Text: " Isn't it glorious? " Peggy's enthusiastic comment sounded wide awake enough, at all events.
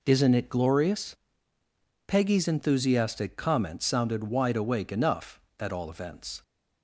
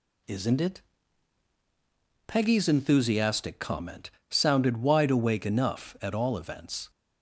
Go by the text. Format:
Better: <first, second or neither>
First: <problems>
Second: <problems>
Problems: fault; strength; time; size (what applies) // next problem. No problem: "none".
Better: first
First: none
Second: skips "glorious"; at 1.1 s // pauses between "comment" and "sounded"; slight; at 4.0 s; 0.22 s long